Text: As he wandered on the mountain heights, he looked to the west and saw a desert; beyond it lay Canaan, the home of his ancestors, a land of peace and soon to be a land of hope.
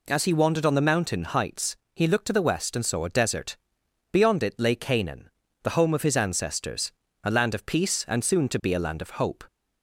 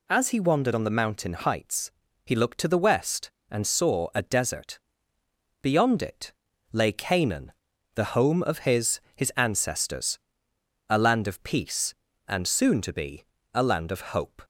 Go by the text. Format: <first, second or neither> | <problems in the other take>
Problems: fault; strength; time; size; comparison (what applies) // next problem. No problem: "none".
first | pauses between "it" and "lay"; at 6.3 s; 0.38 s long // says "his" twice; at 9.1 s // pauses between "be" and "a"; slight; at 13.2 s; 0.28 s long // pauses between "of" and "hope"; slight; at 14.0 s; 0.16 s long